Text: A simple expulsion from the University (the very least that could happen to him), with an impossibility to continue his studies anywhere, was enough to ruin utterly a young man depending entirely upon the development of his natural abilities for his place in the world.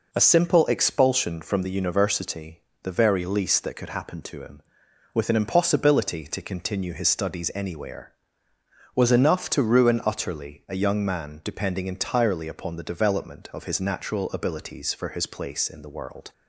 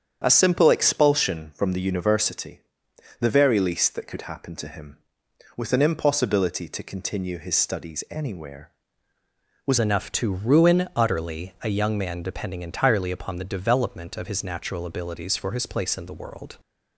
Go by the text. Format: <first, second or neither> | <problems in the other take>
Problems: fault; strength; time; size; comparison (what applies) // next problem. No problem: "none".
first | starts louder than the rest; strong; until 1.2 s; 8.5 dB // changes voice at "enough"; from 9.7 s on; 6.8 s long